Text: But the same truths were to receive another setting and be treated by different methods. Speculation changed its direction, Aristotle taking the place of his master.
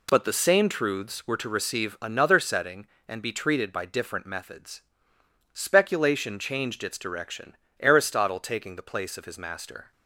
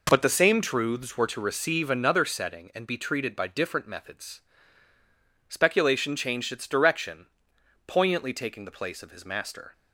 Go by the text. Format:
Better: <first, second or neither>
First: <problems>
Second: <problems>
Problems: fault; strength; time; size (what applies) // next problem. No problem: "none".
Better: first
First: none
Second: says "Poignantly" for "Aristotle"; at 7.8 s